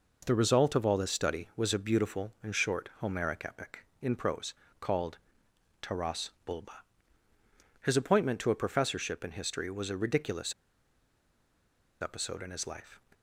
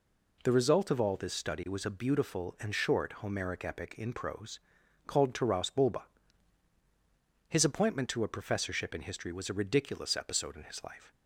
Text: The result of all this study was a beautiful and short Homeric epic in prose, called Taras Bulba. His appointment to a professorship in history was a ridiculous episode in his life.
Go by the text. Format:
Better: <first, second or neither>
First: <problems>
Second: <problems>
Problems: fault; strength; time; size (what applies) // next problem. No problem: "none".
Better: second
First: pauses between "called" and "Taras"; noticeable; at 5.1 s; 0.64 s long // pauses between "Taras" and "Bulba"; slight; at 6.2 s; 0.16 s long // pauses between "ridiculous" and "episode"; strong; at 10.5 s; 1.4 s long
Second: none